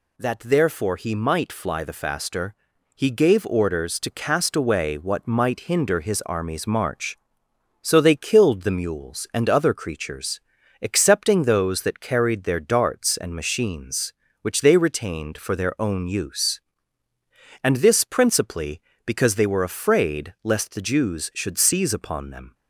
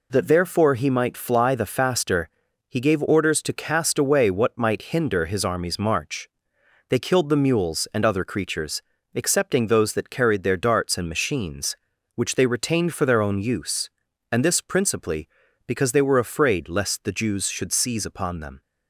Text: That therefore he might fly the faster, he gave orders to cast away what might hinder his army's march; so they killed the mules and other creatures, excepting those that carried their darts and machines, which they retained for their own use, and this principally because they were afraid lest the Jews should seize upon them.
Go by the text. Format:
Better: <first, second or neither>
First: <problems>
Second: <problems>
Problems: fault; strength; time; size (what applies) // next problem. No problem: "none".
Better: first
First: none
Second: skips "so"; at 6.5 s